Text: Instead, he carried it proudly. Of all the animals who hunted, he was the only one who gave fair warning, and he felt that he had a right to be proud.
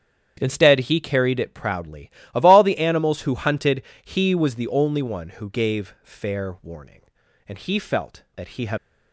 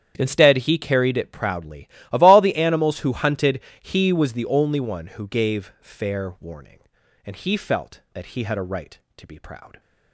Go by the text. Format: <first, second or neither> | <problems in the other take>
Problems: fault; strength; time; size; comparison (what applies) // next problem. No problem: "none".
second | starts louder than the rest; strong; until 1.4 s; 8.5 dB; strong in the second // stops before "a right to be proud"; at 8.7 s